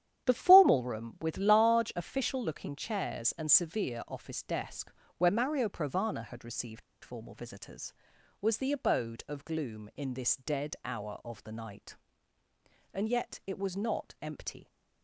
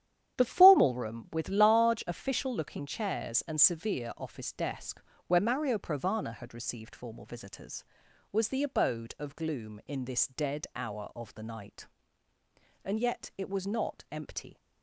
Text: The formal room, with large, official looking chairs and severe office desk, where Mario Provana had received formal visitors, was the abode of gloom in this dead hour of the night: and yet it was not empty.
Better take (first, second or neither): second